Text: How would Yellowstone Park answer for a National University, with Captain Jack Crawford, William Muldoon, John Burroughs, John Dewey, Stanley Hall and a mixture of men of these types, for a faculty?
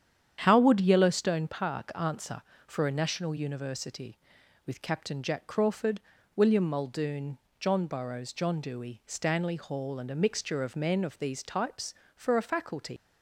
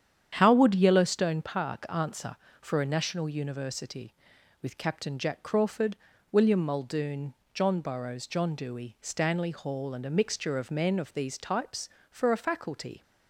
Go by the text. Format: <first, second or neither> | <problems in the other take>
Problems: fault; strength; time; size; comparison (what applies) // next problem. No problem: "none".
second | starts louder than the rest; strong; until 1.4 s; 9 dB; strong in the second // leaves "faculty" unfinished; at 12.9 s; 105 ms